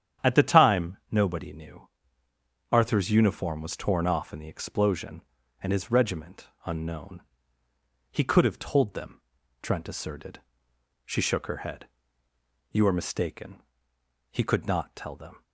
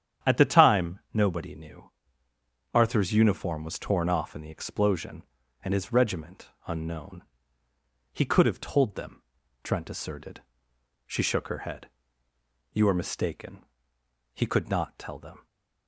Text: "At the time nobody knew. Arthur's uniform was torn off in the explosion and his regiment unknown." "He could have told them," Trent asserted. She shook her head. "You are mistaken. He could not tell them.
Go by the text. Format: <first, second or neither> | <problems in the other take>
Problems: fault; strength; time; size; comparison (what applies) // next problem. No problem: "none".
neither | starts louder than the rest; strong; the same in both // pauses between "time" and "nobody"; slight; the same in both // pauses between "regiment" and "unknown"; slight; the same in both